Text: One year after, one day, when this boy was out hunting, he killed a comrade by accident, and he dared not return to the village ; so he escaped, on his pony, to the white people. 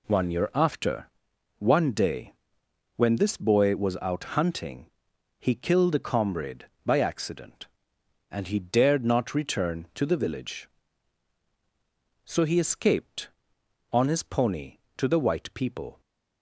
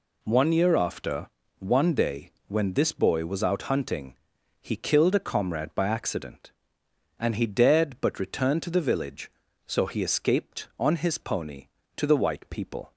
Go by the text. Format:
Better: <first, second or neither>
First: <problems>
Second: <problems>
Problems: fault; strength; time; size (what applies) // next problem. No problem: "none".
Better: first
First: none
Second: says "but" for "not"; at 8.0 s